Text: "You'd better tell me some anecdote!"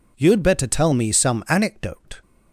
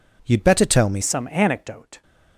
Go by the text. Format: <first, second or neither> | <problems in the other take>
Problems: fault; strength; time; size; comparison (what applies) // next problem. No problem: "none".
first | changes voice at "some"; from 1.0 s on; 1.0 s long